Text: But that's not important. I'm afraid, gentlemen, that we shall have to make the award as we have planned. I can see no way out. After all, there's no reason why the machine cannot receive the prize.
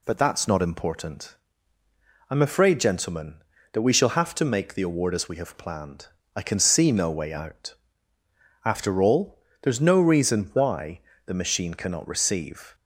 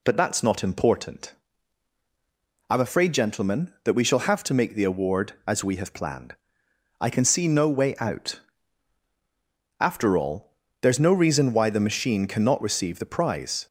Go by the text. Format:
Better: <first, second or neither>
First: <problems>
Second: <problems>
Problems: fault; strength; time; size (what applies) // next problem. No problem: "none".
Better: second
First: pauses between "why" and "the"; slight; at 11.0 s; 0.24 s long // stops before "the prize"; at 12.7 s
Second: none